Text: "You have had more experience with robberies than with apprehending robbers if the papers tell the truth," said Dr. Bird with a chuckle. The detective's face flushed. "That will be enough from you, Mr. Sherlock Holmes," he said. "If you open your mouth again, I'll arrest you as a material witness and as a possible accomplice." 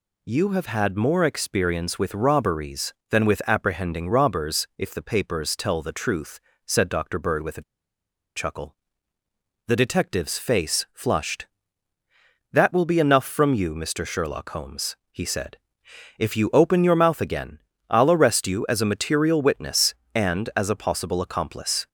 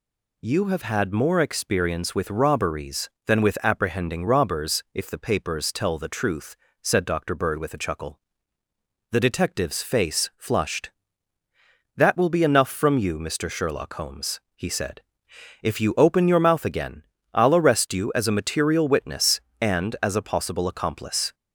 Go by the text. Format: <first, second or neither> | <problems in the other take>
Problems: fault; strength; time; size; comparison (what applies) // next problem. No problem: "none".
second | pauses between "a" and "chuckle"; noticeable; at 7.6 s; 0.74 s long